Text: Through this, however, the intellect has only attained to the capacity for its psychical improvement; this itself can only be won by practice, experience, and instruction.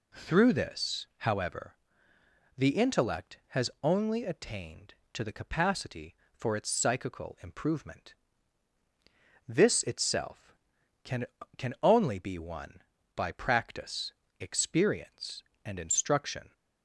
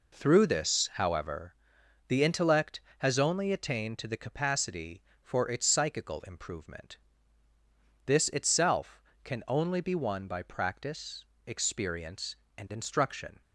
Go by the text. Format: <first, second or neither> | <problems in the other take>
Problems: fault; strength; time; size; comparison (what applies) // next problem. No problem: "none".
second | says "can" twice; at 11.5 s